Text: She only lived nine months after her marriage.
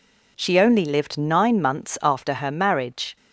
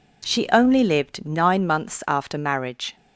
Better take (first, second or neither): first